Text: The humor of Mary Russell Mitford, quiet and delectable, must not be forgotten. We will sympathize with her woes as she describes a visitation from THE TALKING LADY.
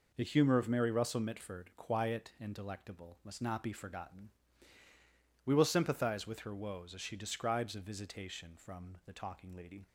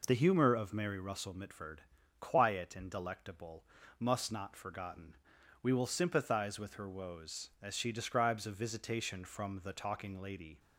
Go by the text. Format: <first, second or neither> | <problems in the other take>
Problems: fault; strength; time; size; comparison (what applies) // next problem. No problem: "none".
first | skips "be"; at 4.5 s